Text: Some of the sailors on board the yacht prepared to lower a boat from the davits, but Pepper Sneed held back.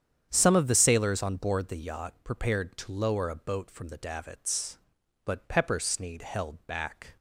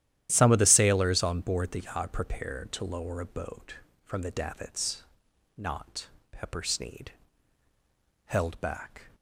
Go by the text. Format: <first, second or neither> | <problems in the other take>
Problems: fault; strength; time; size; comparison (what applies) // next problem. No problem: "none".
first | starts louder than the rest; strong; until 1.3 s; 12 dB; strong in the first // says "not" for "but"; at 5.5 s // pauses between "Sneed" and "held"; at 7.1 s; 1.1 s long